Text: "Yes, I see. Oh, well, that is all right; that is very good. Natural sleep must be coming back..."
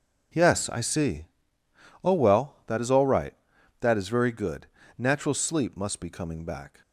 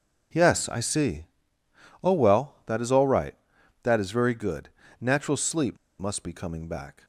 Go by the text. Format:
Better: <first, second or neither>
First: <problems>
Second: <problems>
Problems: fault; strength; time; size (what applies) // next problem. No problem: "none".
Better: first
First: none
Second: pauses between "sleep" and "must"; slight; at 5.7 s; 0.21 s long